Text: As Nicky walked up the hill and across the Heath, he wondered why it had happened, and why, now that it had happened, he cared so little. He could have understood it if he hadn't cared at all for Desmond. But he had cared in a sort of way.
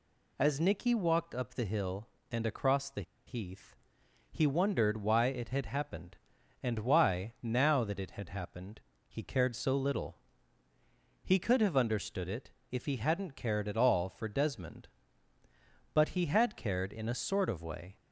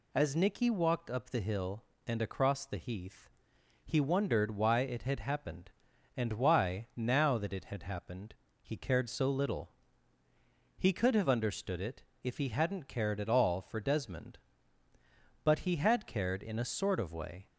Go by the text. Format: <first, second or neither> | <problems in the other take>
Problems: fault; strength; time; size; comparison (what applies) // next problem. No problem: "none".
second | pauses between "the" and "Heath"; slight; at 3.0 s; 0.24 s long // pauses between "it" and "if"; slight; at 12.4 s; 0.20 s long; slight in the second